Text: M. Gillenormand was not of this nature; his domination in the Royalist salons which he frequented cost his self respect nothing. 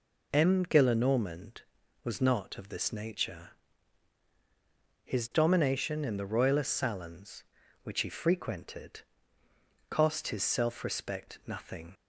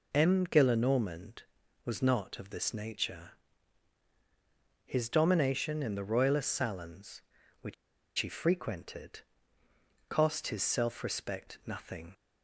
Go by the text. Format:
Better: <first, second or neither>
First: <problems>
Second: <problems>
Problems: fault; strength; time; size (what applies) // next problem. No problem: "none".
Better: first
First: pauses between "frequented" and "cost"; noticeable; at 9.0 s; 0.88 s long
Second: pauses between "which" and "he"; at 7.7 s; 0.44 s long // pauses between "frequented" and "cost"; noticeable; at 9.2 s; 0.88 s long